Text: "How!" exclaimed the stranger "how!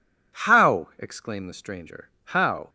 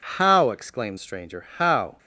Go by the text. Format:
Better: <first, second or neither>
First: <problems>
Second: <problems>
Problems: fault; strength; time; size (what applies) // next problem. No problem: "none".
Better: first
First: none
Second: skips "the"; at 0.9 s